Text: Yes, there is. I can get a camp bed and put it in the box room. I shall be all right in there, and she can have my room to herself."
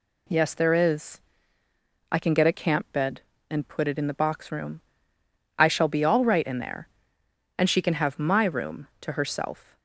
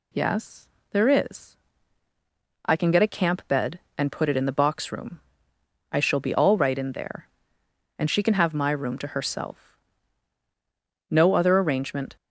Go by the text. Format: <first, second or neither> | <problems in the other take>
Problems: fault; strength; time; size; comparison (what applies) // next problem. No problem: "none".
first | goes on to say "No other arrangement"; noticeable; from 11.0 s on; 1.0 s long